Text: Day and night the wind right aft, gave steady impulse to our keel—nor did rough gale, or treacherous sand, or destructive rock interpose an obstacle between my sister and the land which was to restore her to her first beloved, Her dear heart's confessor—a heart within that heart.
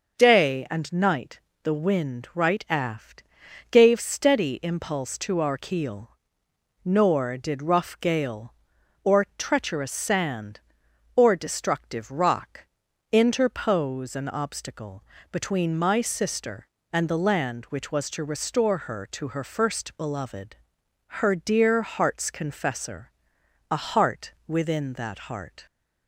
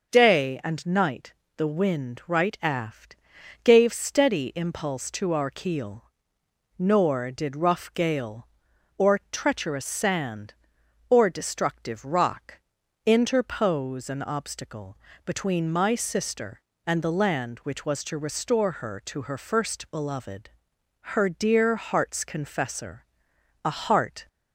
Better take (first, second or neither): first